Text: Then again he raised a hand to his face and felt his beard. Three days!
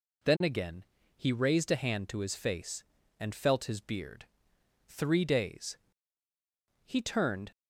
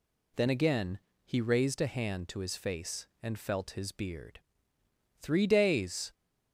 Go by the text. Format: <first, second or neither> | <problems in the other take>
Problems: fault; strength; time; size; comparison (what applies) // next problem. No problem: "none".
second | pauses between "again" and "he"; slight; at 0.8 s; 0.32 s long; slight in the second // goes on to say "He turned"; noticeable; from 6.8 s on; 0.68 s long